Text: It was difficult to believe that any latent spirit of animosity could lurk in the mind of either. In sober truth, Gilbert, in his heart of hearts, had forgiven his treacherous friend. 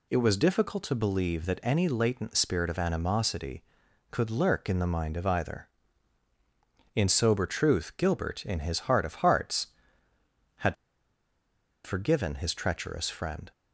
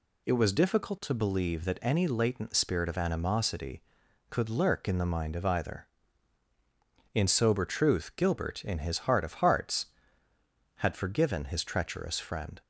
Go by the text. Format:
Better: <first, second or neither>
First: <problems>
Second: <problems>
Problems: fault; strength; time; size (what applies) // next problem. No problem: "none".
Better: second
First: pauses between "had" and "forgiven"; at 10.7 s; 1.1 s long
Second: none